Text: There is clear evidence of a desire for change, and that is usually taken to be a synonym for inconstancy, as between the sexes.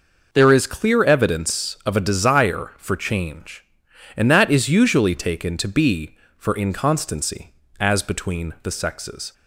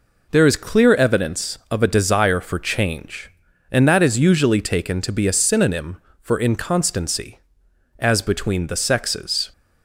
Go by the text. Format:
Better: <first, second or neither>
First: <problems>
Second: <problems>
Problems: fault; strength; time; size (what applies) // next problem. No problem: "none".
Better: second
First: skips "a synonym"; at 6.2 s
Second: none